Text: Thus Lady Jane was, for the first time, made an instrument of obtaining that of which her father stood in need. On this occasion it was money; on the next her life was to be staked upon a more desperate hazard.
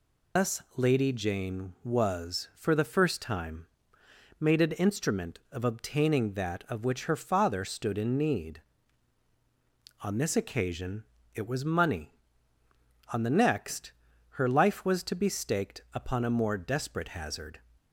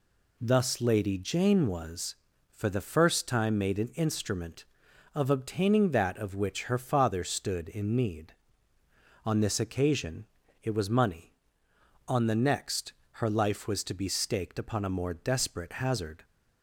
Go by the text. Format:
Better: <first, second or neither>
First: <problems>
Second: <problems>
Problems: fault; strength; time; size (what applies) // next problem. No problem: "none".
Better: second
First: loses the start of "Thus"; at 0.3 s; 65 ms // pauses between "occasion" and "it"; slight; at 11.0 s; 0.30 s long // pauses between "next" and "her"; at 13.9 s; 0.38 s long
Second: pauses between "occasion" and "it"; slight; at 10.2 s; 0.36 s long // pauses between "next" and "her"; slight; at 12.9 s; 0.28 s long